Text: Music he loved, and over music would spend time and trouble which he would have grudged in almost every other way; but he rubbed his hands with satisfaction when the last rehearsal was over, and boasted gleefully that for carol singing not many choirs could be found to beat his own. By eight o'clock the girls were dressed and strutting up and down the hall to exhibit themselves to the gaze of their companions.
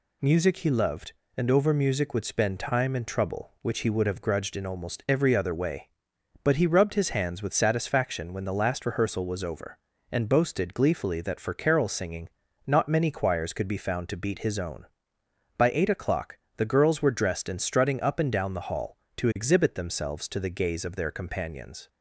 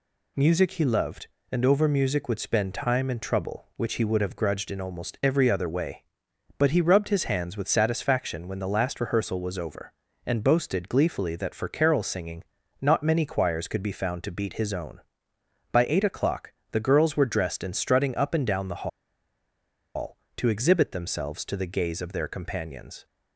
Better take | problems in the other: first | pauses between "singing" and "not"; at 12.4 s; 0.38 s long; also in the first // pauses between "o'clock" and "the"; slight; at 16.5 s; 0.16 s long; slight in the first // pauses between "the" and "hall"; at 18.8 s; 1.0 s long

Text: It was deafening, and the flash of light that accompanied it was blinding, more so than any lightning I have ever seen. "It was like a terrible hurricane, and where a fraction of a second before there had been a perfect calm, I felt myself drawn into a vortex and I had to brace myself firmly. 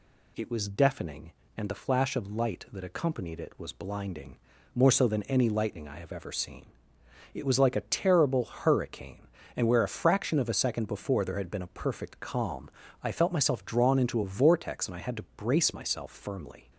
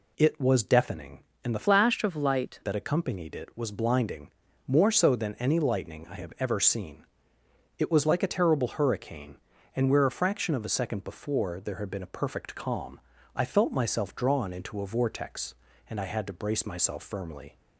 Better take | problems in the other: first | changes voice from "flash" to "light"; from 1.6 to 2.5 s; 0.9 s long

